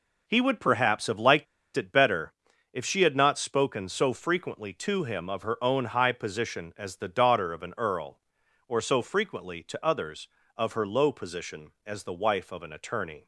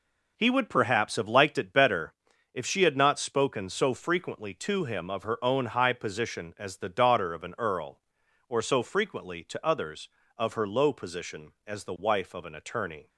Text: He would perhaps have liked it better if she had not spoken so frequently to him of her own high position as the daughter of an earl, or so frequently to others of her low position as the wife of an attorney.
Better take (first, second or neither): second